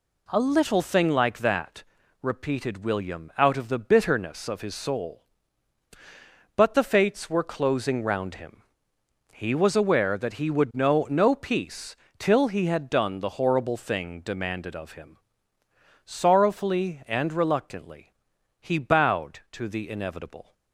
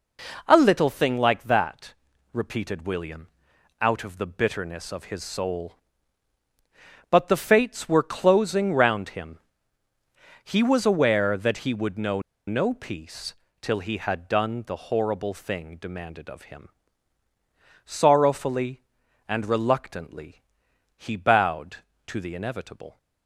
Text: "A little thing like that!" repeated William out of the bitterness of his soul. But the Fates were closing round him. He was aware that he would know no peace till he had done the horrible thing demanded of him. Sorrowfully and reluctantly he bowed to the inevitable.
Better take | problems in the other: first | pauses between "William" and "out"; noticeable; at 3.2 s; 0.50 s long // pauses between "know" and "no"; slight; at 12.1 s; 0.27 s long // pauses between "peace" and "till"; slight; at 13.3 s; 0.28 s long; slight in the first // pauses between "reluctantly" and "he"; noticeable; at 20.4 s; 0.56 s long; noticeable in the first

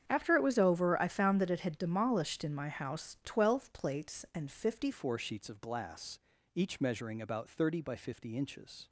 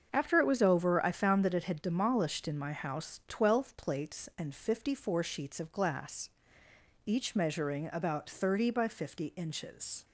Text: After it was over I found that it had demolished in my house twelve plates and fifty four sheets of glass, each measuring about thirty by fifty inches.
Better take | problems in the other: second | starts louder than the rest; strong; until 1.0 s; 8.5 dB; also in the second // changes voice at "four"; from 4.9 s on; 3.9 s long

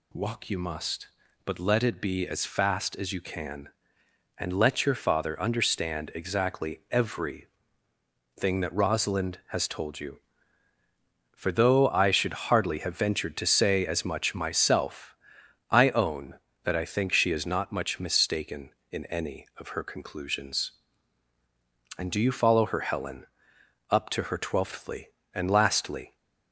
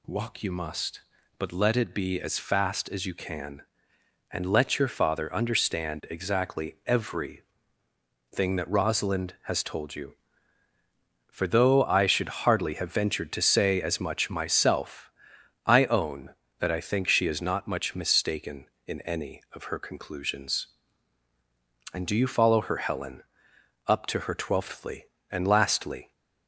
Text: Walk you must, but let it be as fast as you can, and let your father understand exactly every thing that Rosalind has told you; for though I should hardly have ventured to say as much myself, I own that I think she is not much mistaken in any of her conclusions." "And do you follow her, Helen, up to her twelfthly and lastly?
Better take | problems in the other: neither | pauses between "every" and "thing"; noticeable; the same in both

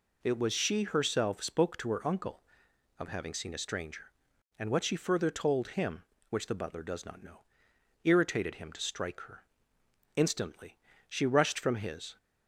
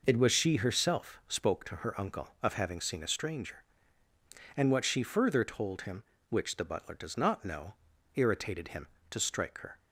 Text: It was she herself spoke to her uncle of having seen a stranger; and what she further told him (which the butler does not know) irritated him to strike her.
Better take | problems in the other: second | goes on to say "Instantly she rushed from his"; strong; from 10.1 s on; 2.0 s long

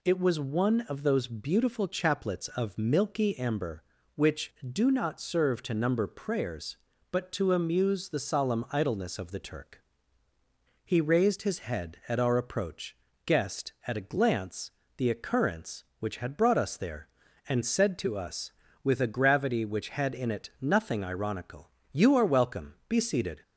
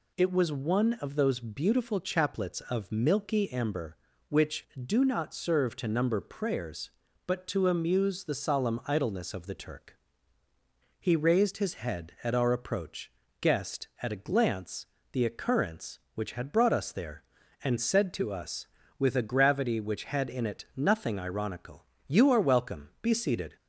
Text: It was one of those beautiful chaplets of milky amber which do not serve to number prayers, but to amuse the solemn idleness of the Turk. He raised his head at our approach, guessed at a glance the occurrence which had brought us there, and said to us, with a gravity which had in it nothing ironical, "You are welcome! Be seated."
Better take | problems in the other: neither | pauses between "glance" and "the"; slight; the same in both

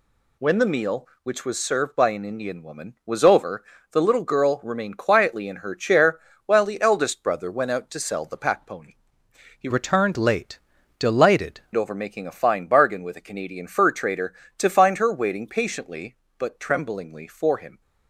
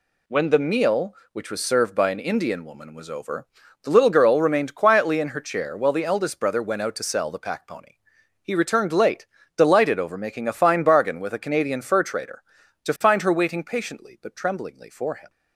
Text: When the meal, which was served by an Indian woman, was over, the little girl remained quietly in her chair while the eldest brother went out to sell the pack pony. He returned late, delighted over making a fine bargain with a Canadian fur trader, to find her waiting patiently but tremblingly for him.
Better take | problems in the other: second | pauses between "chair" and "while"; slight; at 6.1 s; 0.26 s long // changes voice from "returned" to "delighted"; from 9.7 to 11.6 s; 1.9 s long

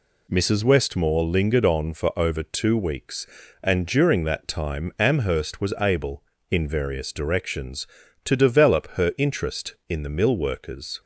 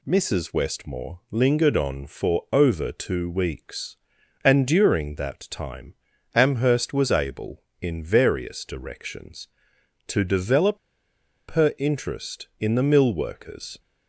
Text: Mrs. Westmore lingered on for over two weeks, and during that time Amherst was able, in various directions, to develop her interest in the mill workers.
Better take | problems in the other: first | pauses between "time" and "Amherst"; at 5.9 s; 0.40 s long // pauses between "develop" and "her"; noticeable; at 10.7 s; 0.72 s long

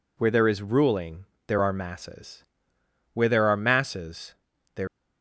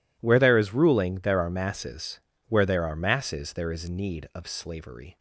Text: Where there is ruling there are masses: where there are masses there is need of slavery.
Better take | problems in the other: second | pauses between "ruling" and "there"; slight; at 1.2 s; 0.20 s long // pauses between "masses" and "there"; at 4.3 s; 0.42 s long // stops before "is need of slavery"; at 4.8 s

